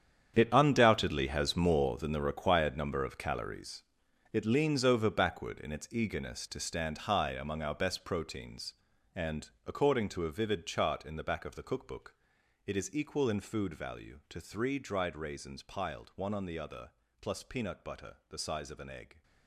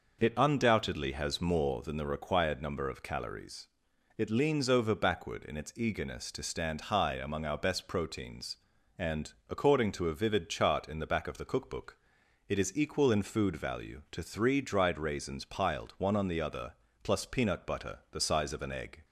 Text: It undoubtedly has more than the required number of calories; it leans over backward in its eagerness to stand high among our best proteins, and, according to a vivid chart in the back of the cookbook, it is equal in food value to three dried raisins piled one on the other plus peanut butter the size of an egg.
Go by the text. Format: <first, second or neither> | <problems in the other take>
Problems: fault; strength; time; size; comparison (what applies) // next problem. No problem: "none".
second | gets quieter; strong; throughout; 14 dB // pauses between "other" and "plus"; slight; at 16.9 s; 0.30 s long; slight in the second